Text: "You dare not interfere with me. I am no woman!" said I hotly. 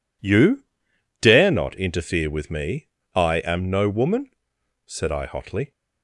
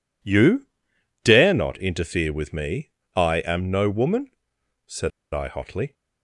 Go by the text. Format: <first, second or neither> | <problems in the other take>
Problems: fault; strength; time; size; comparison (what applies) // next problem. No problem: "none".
first | pauses between "You" and "dare"; noticeable; at 0.6 s; 0.56 s long; noticeable in the first // pauses between "said" and "I"; slight; at 5.1 s; 0.22 s long